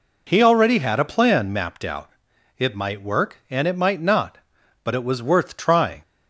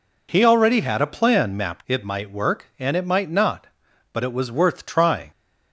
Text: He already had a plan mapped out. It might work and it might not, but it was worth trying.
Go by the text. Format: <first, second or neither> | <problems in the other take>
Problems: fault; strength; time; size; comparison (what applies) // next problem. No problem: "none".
first | skips "out"; at 1.8 s